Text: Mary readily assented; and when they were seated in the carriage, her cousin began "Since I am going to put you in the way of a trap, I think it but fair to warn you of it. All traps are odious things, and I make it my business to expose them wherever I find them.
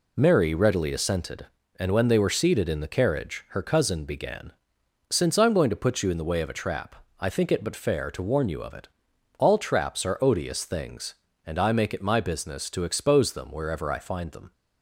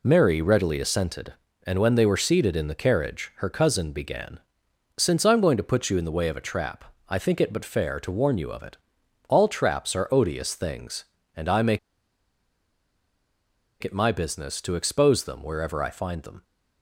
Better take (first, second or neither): first